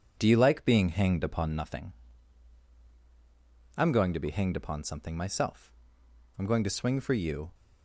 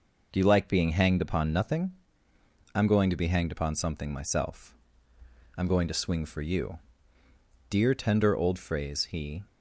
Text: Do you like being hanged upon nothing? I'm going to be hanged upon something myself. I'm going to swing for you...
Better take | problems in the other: first | goes on to say "Dear tender old phrase he"; strong; from 7.6 s on; 1.7 s long

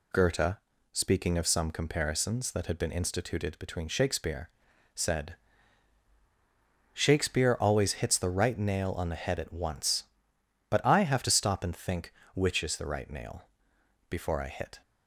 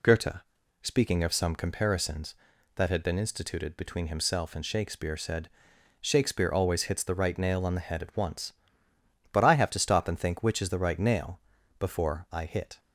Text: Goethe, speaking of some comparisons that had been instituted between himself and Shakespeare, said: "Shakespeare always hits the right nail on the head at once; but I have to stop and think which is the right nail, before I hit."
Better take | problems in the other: second | skips "himself and"; at 3.8 s

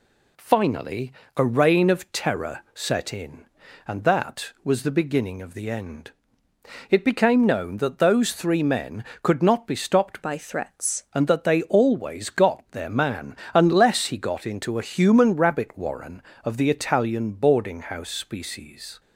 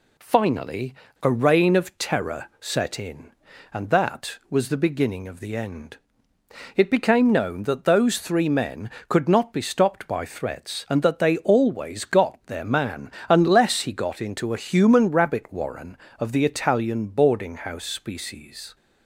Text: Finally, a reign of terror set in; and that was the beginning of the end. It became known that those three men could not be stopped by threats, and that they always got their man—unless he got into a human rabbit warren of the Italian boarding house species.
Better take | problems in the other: second | changes voice from "by" to "threats"; from 10.2 to 11.0 s; 0.8 s long

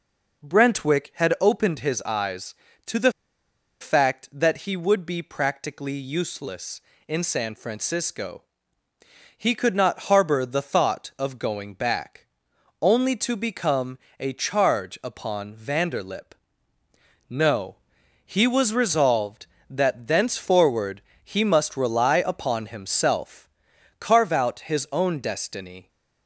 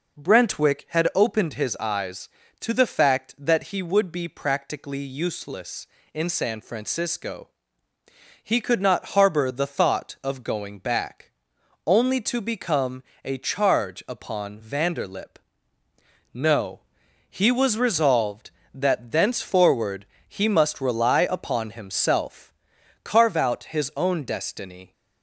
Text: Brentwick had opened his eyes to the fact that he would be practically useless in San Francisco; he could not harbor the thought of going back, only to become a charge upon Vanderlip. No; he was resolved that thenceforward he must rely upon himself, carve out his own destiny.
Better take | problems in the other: second | pauses between "the" and "fact"; noticeable; at 3.1 s; 0.69 s long // pauses between "become" and "a"; slight; at 13.9 s; 0.18 s long; slight in the second // pauses between "thenceforward" and "he"; slight; at 21.0 s; 0.22 s long; slight in the second

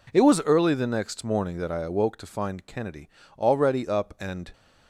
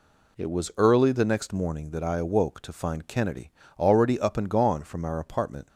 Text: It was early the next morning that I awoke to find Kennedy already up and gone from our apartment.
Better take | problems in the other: second | pauses between "Kennedy" and "already"; slight; at 3.0 s; 0.30 s long; slight in the second // stops before "gone from our apartment"; at 4.5 s

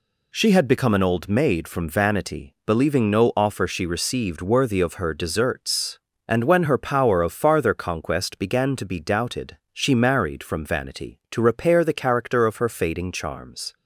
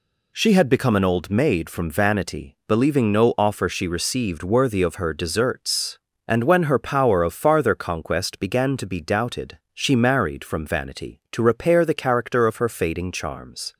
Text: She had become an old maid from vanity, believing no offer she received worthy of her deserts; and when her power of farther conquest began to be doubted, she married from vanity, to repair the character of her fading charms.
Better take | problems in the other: neither | none

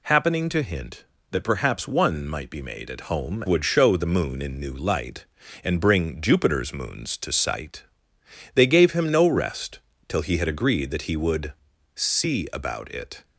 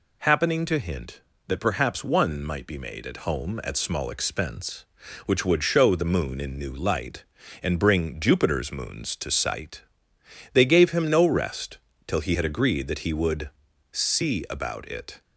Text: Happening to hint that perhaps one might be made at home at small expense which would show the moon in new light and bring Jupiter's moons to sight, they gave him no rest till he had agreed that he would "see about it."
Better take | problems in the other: second | skips "at small expense which"; at 3.4 s // pauses between "rest" and "till"; slight; at 9.7 s; 0.28 s long; slight in the second // pauses between "would" and "see"; at 11.5 s; 0.42 s long; also in the second

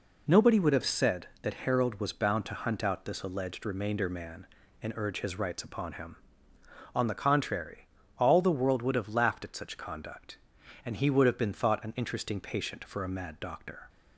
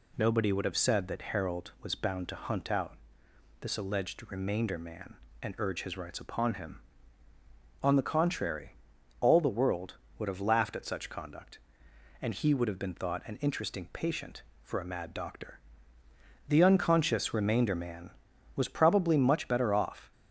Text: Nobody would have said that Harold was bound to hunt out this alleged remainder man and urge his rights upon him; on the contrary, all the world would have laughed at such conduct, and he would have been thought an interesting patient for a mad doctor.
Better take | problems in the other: first | pauses between "out" and "this"; noticeable; at 2.9 s; 0.66 s long // goes on to say "The unconscious remainder man was probably much better off"; strong; from 16.4 s on; 3.6 s long

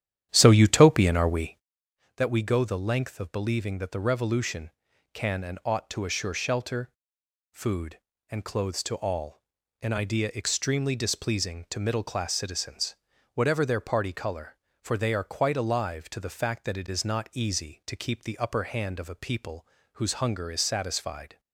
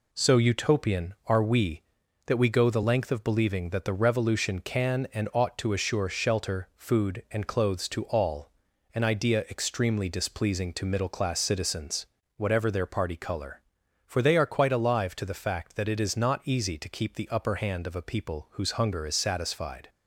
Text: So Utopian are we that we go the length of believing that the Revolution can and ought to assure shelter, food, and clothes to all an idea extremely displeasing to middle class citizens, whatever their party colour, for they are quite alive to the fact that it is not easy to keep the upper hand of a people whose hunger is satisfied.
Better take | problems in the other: second | starts louder than the rest; strong; until 1.9 s; 10.5 dB // pauses between "all" and "an"; at 9.4 s; 0.40 s long; also in the second // pauses between "people" and "whose"; slight; at 19.6 s; 0.28 s long

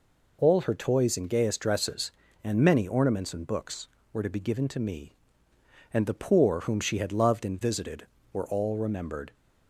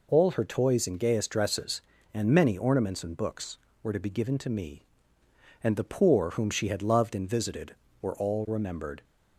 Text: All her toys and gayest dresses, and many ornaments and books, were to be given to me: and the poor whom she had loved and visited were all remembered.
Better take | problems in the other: neither | none

